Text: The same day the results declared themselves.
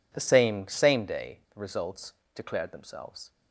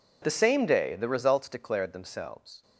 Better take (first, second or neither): second